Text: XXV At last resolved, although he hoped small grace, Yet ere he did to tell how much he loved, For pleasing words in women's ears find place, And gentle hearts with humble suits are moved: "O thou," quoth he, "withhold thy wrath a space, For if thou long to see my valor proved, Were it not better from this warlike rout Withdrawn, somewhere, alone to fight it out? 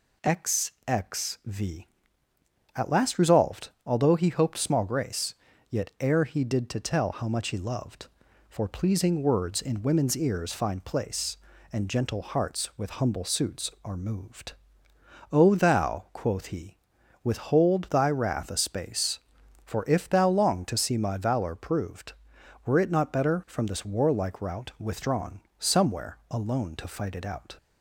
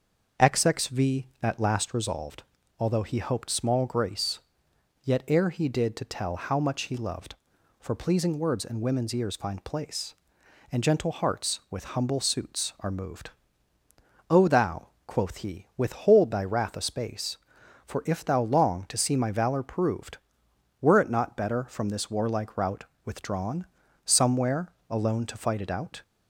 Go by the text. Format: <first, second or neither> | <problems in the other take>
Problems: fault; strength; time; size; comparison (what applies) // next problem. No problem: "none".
first | starts louder than the rest; until 2.2 s; 6.5 dB // pauses between "rout" and "Withdrawn"; slight; at 22.8 s; 0.18 s long